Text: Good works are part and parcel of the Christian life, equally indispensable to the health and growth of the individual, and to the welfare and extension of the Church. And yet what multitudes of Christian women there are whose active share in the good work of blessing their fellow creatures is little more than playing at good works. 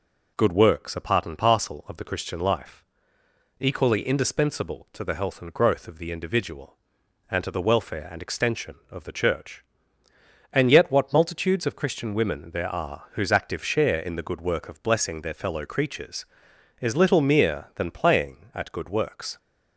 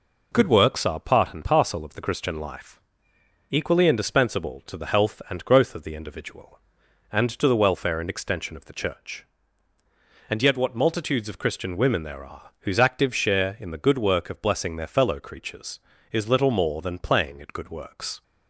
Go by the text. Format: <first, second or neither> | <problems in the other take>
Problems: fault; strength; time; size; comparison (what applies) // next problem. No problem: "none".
second | says "mere" for "more"; at 17.2 s